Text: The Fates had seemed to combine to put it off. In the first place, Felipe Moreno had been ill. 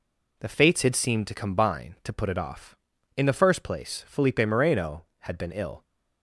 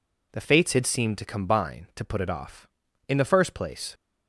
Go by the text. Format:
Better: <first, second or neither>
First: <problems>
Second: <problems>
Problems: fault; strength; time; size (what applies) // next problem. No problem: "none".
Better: first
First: none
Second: stops before "Felipe Moreno had been ill"; at 3.9 s